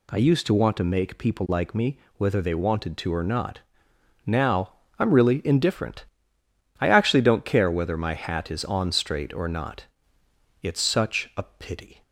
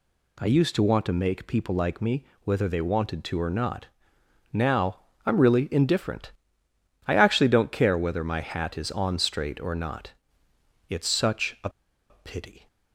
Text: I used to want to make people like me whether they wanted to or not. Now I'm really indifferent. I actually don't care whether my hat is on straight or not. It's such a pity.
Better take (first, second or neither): first